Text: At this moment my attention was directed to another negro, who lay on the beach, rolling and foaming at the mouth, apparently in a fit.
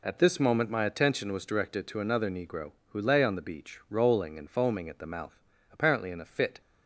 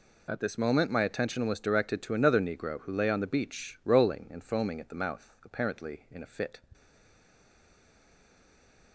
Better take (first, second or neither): first